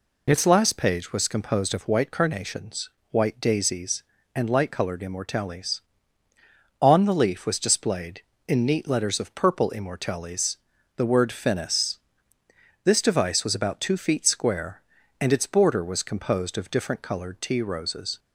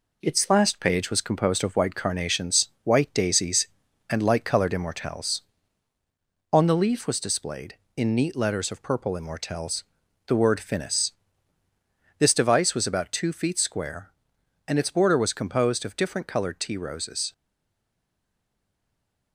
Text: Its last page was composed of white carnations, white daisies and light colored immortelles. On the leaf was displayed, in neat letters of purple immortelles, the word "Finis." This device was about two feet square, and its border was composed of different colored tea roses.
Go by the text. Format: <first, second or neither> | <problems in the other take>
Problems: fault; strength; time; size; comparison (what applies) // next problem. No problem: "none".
first | stays silent after the last word; noticeable; from 17.3 s on; 2.0 s long